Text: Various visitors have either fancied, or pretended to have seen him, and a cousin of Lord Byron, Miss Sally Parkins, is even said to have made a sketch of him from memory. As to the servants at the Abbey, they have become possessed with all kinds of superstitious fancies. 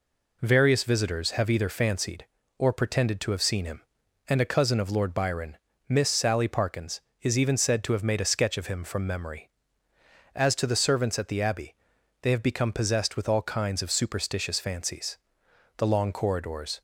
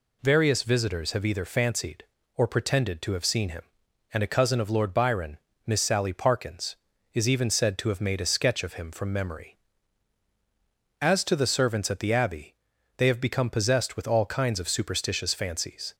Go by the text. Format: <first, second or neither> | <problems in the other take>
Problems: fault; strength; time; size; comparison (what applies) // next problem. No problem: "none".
second | goes on to say "The long corridors"; noticeable; from 15.7 s on; 1.0 s long